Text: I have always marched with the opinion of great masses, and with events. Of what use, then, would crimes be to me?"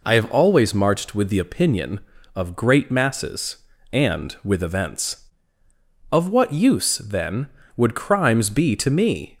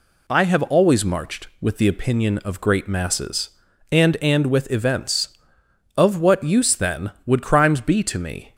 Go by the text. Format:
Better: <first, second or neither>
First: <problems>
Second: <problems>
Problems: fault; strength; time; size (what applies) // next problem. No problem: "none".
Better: first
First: none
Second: says "and" twice; at 4.2 s